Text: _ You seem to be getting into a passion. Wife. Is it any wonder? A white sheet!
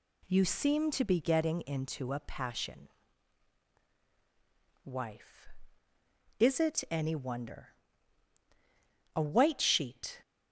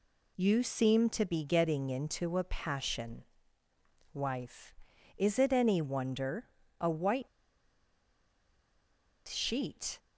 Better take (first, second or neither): first